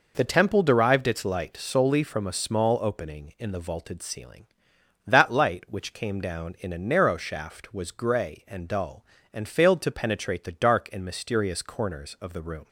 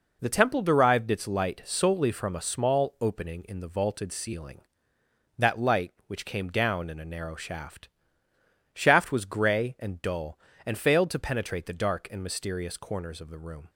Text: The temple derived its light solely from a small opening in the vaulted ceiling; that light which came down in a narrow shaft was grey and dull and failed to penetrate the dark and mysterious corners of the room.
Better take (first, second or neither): first